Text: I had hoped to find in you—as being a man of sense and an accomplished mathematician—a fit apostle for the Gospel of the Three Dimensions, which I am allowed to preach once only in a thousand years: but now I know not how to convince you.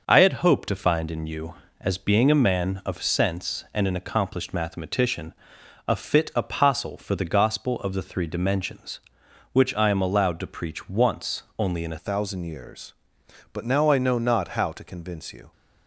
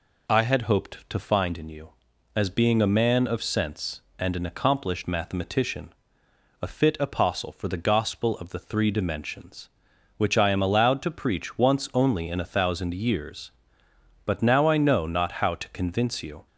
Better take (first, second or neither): second